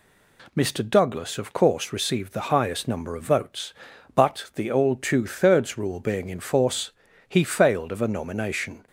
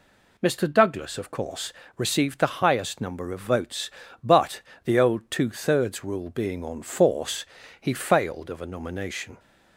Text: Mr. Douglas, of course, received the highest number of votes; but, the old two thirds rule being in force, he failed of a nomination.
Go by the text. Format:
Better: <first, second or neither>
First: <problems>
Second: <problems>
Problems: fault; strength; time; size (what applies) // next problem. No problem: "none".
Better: first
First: none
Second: says "on" for "in"; at 6.6 s